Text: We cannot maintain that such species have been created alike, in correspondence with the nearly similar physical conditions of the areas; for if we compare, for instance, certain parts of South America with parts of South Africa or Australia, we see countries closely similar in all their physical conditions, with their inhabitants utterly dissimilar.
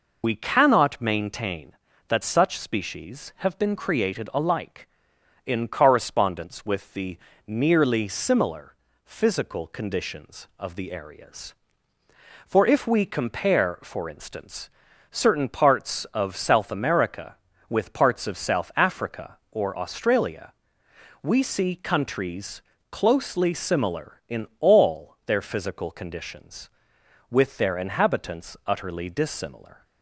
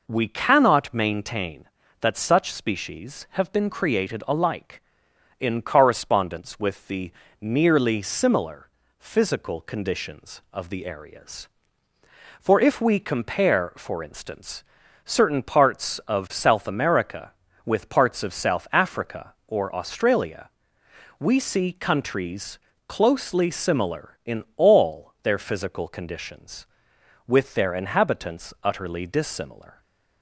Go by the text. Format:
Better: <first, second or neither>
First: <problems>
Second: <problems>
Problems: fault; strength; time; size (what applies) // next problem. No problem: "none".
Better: second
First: loses the start of "We"; at 0.2 s; 80 ms // pauses between "the" and "nearly"; slight; at 7.1 s; 0.30 s long // pauses between "similar" and "physical"; slight; at 8.7 s; 0.30 s long // pauses between "countries" and "closely"; slight; at 22.6 s; 0.26 s long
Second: pauses between "the" and "nearly"; slight; at 7.0 s; 0.30 s long // pauses between "similar" and "physical"; slight; at 8.6 s; 0.30 s long // pauses between "countries" and "closely"; slight; at 22.6 s; 0.26 s long